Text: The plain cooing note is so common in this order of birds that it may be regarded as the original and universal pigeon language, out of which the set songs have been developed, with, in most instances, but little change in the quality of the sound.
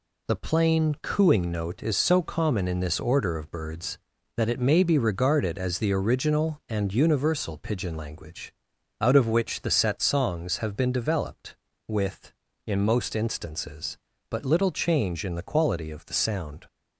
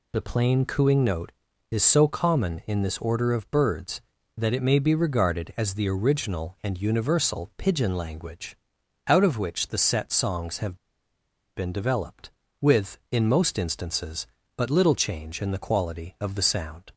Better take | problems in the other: first | pauses between "have" and "been"; noticeable; at 10.7 s; 0.79 s long

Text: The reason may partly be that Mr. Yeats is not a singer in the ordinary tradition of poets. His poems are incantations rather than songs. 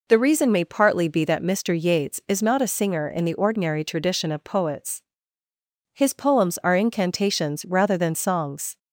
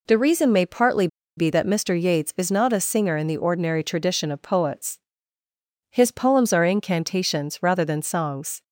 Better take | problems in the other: first | pauses between "partly" and "be"; slight; at 1.0 s; 0.30 s long

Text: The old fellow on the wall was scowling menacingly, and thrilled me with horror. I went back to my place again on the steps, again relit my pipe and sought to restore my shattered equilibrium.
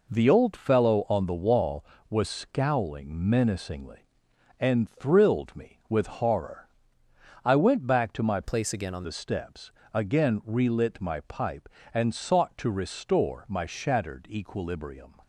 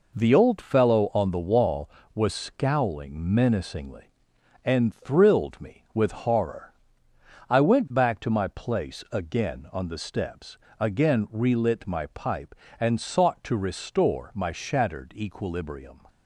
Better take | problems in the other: second | changes voice from "place" to "on"; from 8.4 to 9.0 s; 0.6 s long

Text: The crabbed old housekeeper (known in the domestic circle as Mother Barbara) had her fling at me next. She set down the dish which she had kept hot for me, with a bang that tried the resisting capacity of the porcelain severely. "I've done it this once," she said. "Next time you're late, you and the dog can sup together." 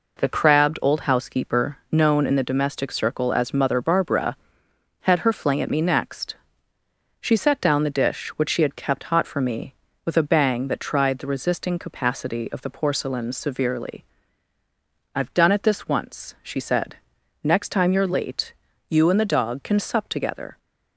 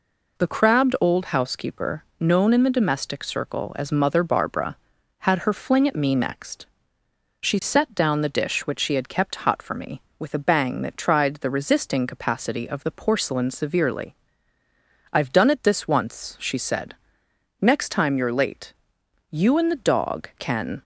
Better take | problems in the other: first | stops before "sup together"; at 20.7 s

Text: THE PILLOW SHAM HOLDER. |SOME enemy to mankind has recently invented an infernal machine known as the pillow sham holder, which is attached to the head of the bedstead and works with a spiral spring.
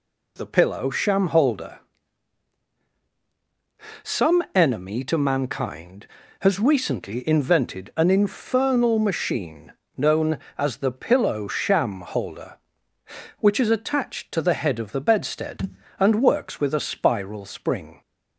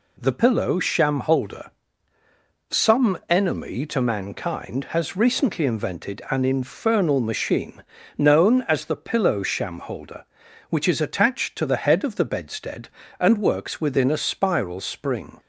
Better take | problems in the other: first | pauses between "machine" and "known"; slight; at 7.8 s; 0.34 s long; slight in the first // says "within" for "with"; at 13.7 s

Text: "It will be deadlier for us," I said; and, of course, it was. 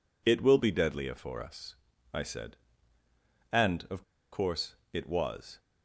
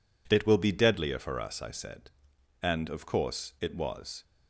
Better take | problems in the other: second | pauses between "of" and "course"; slight; at 4.0 s; 0.30 s long

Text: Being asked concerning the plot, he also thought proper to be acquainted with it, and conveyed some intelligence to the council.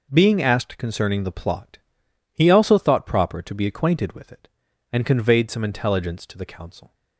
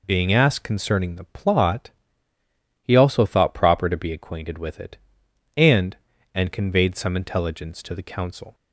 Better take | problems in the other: first | says "and" twice; at 6.3 s

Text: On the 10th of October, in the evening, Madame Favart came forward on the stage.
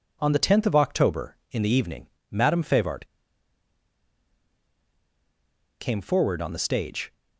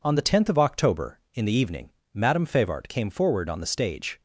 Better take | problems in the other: second | pauses between "Favart" and "came"; strong; at 3.0 s; 2.7 s long

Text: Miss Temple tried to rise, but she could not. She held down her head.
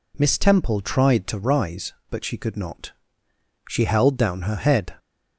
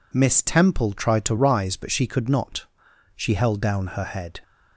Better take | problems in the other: neither | none

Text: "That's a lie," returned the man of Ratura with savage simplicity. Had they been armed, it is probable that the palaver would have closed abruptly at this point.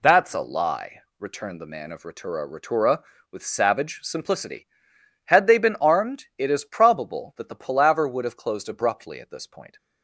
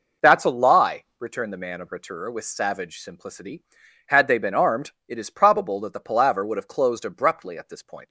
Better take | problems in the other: second | says "Ratura" twice; at 2.4 s

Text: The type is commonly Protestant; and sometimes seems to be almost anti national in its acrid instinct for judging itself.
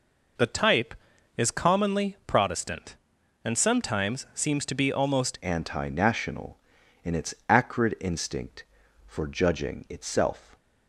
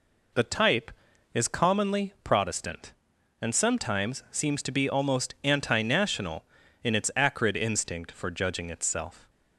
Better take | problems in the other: second | changes voice at "anti"; from 5.4 s on; 5.1 s long // pauses between "its" and "acrid"; slight; at 7.3 s; 0.16 s long

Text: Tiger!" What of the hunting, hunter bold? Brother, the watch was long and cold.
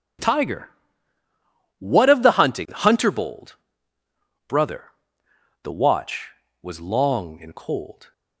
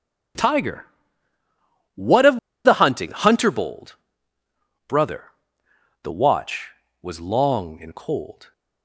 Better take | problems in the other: first | pauses between "of" and "the"; slight; at 2.3 s; 0.26 s long

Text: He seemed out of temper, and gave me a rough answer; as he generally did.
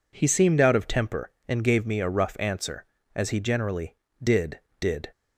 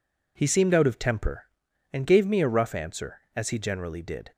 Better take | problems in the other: second | says "did" twice; at 4.7 s

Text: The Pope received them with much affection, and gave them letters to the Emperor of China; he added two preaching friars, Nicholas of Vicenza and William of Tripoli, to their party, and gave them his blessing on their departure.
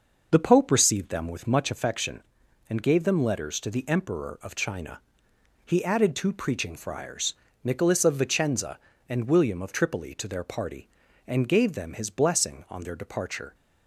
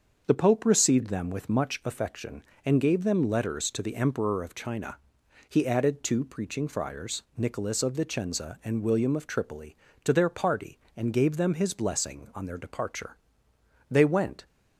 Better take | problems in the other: first | starts louder than the rest; until 1.2 s; 6.5 dB; noticeable in the first // goes on to say "They went"; from 13.8 s on; 0.56 s long

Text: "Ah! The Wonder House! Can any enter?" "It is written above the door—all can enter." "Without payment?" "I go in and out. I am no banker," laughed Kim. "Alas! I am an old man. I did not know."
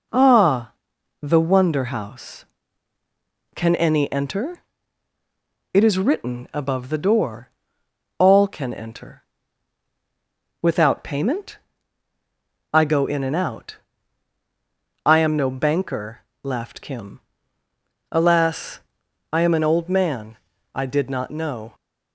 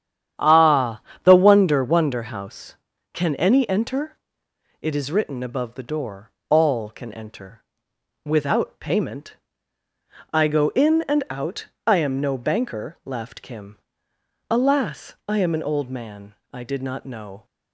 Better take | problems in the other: first | starts louder than the rest; strong; until 1.6 s; 9.5 dB // says "Wonder" twice; at 1.8 s

